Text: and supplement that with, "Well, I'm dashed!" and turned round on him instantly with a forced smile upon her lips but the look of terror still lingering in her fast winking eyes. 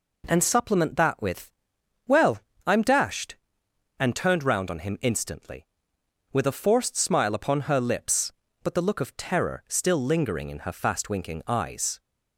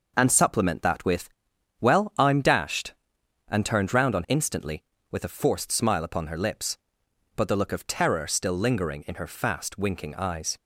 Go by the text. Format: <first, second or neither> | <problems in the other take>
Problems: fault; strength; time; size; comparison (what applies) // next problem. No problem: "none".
first | skips "him"; at 4.2 s